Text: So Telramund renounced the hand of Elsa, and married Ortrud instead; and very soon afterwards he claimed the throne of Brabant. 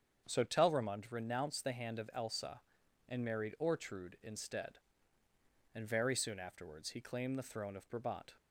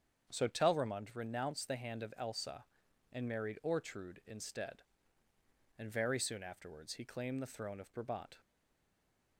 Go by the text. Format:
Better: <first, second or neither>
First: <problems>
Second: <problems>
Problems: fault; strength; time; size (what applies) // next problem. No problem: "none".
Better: first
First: starts louder than the rest; strong; until 1.3 s; 7.5 dB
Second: starts louder than the rest; strong; until 1.3 s; 7.5 dB // stays silent after the last word; from 8.4 s on; 0.9 s long